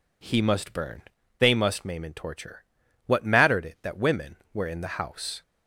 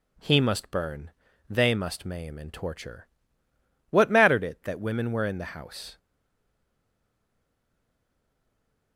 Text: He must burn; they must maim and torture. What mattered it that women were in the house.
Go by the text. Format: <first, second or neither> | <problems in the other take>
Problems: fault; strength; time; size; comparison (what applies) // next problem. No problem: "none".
first | stays silent after the last word; strong; from 5.9 s on; 3.0 s long